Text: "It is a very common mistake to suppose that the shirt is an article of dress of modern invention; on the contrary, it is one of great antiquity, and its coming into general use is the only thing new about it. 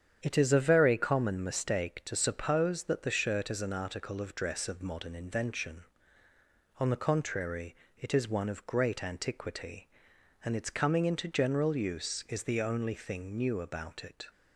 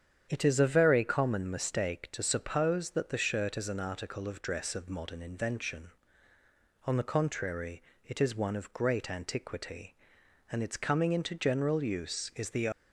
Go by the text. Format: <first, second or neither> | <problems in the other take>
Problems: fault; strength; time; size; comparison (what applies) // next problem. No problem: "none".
first | starts louder than the rest; strong; until 1.3 s; 8.5 dB; strong in the first // stops before "only thing new about it"; at 12.7 s